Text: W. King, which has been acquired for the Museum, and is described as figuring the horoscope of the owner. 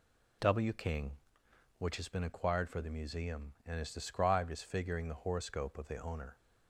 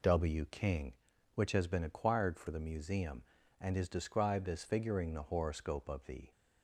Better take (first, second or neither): first